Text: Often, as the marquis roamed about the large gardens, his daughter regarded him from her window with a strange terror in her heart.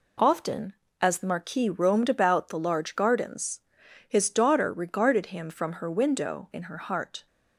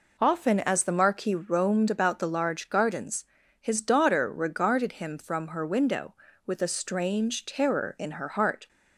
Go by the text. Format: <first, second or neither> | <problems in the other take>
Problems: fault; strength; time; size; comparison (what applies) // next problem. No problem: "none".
second | skips "with a strange terror"; at 6.5 s